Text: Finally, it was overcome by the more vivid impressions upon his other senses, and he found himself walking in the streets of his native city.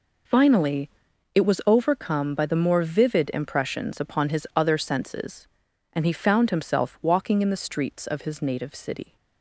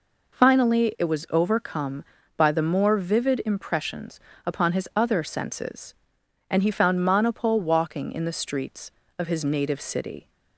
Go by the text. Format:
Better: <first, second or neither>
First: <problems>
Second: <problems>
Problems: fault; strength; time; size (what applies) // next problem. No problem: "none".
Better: first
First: none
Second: pauses between "impressions" and "upon"; slight; at 4.1 s; 0.26 s long // says "monopole" for "himself"; at 7.0 s